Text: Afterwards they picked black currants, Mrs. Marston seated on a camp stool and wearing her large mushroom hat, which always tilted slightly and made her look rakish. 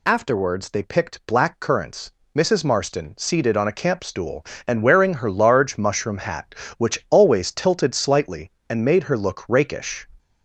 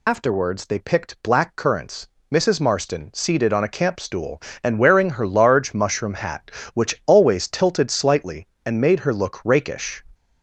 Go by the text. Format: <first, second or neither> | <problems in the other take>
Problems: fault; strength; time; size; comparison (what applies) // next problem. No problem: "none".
first | loses the start of "Afterwards"; at 0.0 s; 45 ms